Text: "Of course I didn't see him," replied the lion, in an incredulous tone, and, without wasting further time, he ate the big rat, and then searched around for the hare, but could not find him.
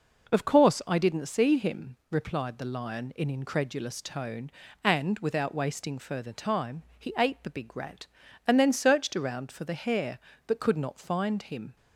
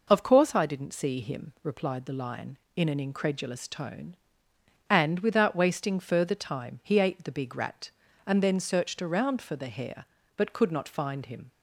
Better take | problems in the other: second | skips "an"; at 3.2 s

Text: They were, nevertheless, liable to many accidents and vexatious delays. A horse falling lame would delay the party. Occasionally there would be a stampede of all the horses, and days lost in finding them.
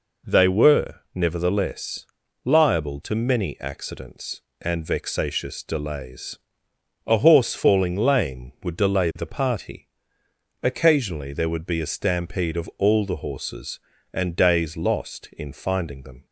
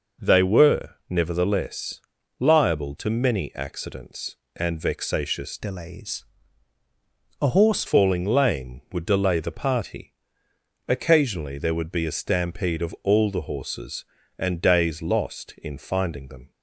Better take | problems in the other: first | changes voice from "delays" to "horse"; from 5.5 to 7.8 s; 2.3 s long

